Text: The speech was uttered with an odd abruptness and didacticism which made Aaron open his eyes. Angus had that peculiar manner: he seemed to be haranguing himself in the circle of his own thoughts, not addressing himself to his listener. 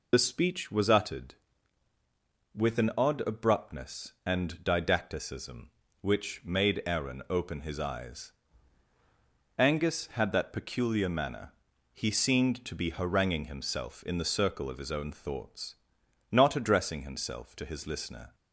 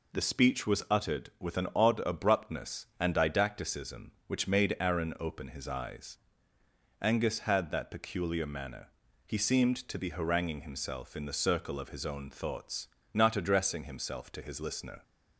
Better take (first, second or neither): second